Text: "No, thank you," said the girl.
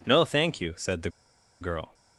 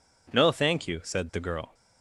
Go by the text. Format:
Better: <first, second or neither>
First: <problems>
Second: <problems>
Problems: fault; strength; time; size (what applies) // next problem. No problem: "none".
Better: second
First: pauses between "the" and "girl"; noticeable; at 1.0 s; 0.51 s long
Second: none